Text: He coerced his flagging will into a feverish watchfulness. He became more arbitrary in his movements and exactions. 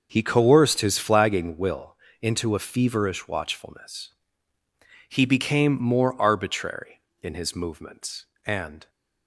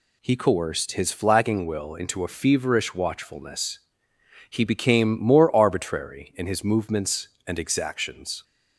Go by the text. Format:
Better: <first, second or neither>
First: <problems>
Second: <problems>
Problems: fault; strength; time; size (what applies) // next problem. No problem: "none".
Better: second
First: starts louder than the rest; noticeable; until 1.1 s; 6 dB // pauses between "will" and "into"; slight; at 1.9 s; 0.26 s long // stops before "exactions"; at 8.8 s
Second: none